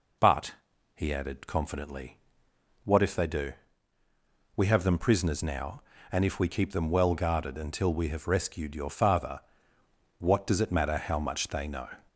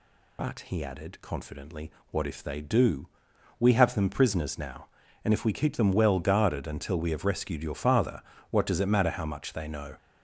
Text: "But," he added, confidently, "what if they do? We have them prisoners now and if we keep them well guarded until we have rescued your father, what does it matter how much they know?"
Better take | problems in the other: first | loses the start of "But"; at 0.3 s; 35 ms

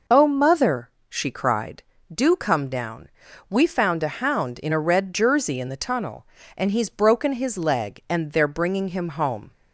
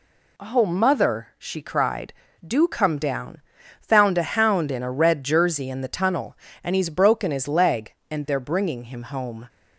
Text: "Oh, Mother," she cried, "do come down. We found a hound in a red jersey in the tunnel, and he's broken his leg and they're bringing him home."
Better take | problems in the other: first | skips "We"; at 3.6 s

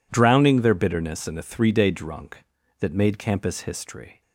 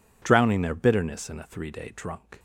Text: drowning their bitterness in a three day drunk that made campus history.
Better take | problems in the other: first | stops before "that made campus history"; at 2.3 s

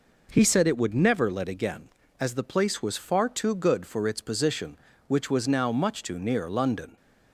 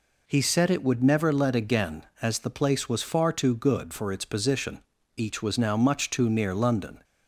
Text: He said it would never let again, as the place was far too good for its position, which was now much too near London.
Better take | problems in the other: first | says "each" for "which"; at 5.1 s

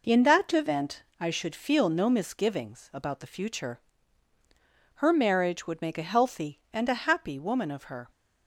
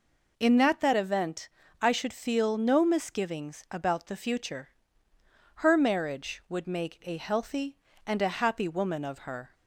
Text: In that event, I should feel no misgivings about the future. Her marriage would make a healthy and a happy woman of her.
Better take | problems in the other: first | says "that" twice; at 0.8 s

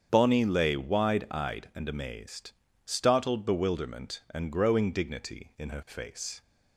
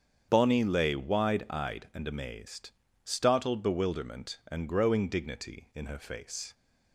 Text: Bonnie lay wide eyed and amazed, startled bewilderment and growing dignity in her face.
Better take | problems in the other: neither | starts louder than the rest; strong; the same in both

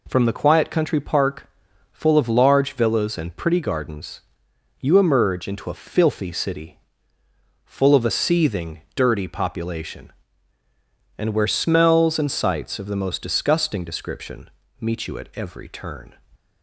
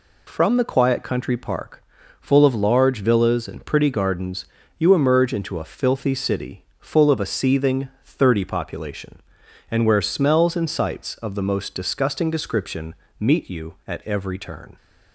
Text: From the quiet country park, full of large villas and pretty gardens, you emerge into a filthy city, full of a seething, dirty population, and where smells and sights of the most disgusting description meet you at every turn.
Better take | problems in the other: first | says "thirty" for "dirty"; at 8.0 s // pauses between "description" and "meet"; slight; at 12.9 s; 0.24 s long; slight in the first

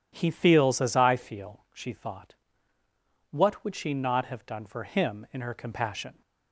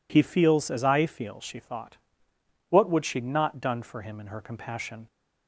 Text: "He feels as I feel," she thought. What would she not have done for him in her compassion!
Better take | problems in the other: first | skips "have"; at 3.6 s

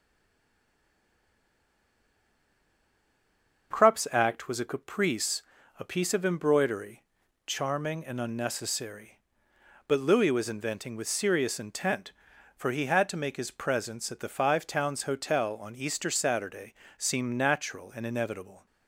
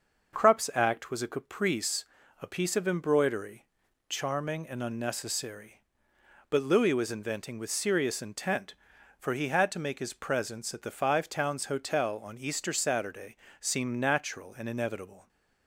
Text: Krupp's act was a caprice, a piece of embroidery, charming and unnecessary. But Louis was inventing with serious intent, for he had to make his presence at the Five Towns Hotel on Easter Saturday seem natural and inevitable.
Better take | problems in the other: second | stays silent before the first word; strong; until 3.7 s; 3.7 s long // starts louder than the rest; until 4.7 s; 6 dB; also in the second // pauses between "Saturday" and "seem"; slight; at 16.7 s; 0.24 s long; slight in the second

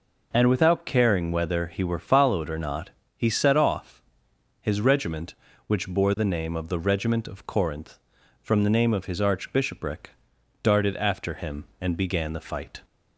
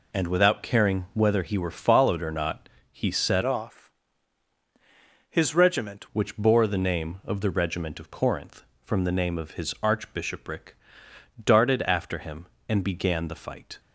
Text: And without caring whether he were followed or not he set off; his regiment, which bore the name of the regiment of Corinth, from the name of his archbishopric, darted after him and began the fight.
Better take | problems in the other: first | pauses between "not" and "he"; slight; at 2.6 s; 0.22 s long; slight in the first // changes voice from "off" to "regiment"; from 3.4 to 6.0 s; 2.6 s long

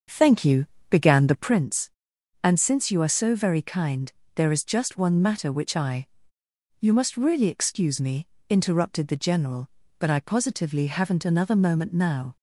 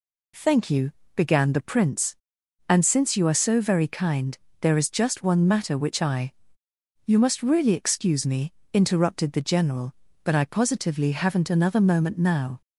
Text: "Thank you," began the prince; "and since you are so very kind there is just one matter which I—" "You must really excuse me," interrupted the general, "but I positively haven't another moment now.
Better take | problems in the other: second | starts louder than the rest; until 1.6 s; 6.5 dB // pauses between "kind" and "there"; slight; at 4.1 s; 0.24 s long; slight in the second

